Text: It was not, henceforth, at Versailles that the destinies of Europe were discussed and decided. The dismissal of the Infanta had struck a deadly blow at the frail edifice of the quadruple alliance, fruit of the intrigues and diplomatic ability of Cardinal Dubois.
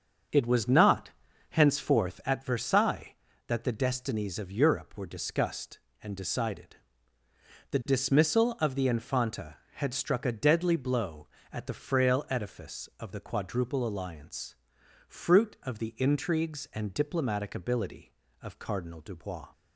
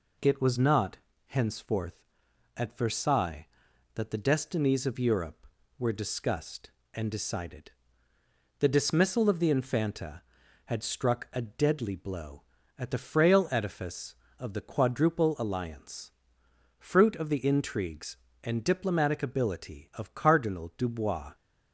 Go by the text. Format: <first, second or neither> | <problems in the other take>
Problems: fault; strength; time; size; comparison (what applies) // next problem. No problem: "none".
second | starts louder than the rest; until 2.1 s; 6 dB